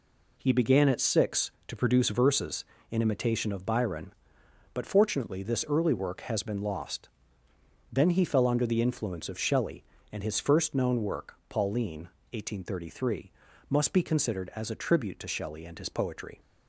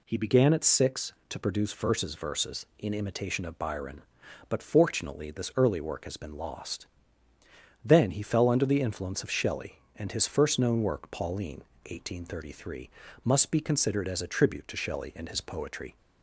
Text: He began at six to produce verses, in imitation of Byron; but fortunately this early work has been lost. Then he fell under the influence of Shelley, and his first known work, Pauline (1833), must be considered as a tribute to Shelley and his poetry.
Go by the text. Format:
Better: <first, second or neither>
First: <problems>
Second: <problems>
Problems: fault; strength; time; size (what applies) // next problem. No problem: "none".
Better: first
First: none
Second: says "verses" twice; at 2.1 s